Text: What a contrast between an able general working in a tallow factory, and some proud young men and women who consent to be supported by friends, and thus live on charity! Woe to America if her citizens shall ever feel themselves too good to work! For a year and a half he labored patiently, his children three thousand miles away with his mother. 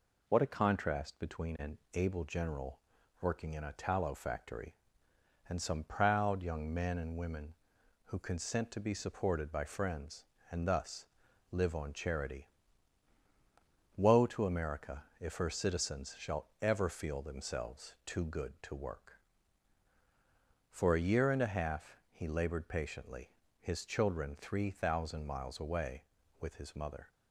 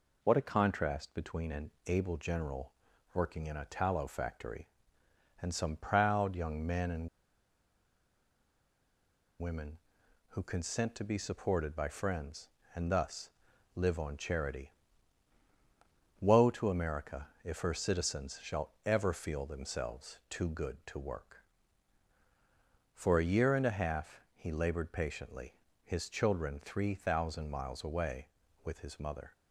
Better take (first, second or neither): first